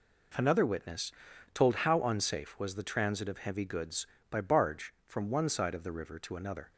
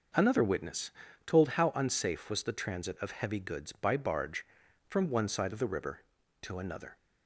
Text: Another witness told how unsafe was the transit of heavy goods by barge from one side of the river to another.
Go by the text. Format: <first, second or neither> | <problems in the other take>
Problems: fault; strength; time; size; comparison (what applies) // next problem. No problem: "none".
neither | pauses between "witness" and "told"; the same in both